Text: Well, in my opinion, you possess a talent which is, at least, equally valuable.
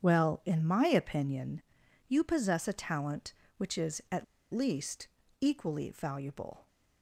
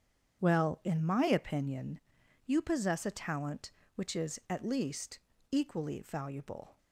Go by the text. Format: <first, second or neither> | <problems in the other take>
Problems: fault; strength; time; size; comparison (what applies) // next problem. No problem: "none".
second | starts louder than the rest; strong; until 1.0 s; 8 dB; strong in the second // pauses between "at" and "least"; slight; at 4.2 s; 0.28 s long